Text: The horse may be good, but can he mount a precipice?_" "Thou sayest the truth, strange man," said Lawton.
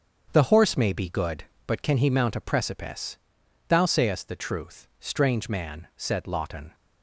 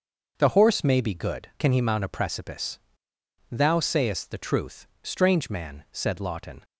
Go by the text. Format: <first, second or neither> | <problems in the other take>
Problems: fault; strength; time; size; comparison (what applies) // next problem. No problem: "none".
first | starts louder than the rest; until 1.3 s; 6.5 dB; strong in the first // skips "but"; at 1.5 s